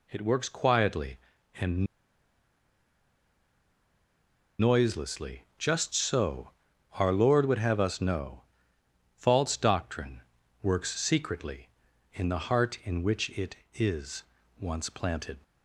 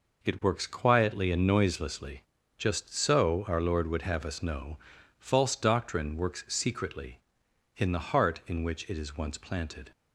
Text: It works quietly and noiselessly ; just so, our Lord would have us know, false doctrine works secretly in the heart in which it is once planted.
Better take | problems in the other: second | pauses between "and" and "noiselessly"; strong; at 1.8 s; 2.7 s long // pauses between "doctrine" and "works"; at 10.2 s; 0.40 s long // pauses between "is" and "once"; slight; at 14.2 s; 0.36 s long

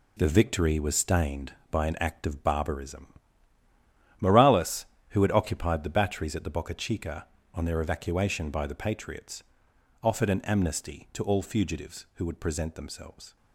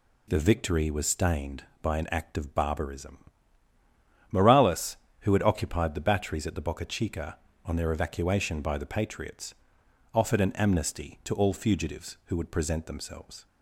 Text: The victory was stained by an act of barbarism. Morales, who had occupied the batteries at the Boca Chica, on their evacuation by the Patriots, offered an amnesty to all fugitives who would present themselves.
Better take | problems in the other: second | gets quieter; strong; throughout; 8.5 dB

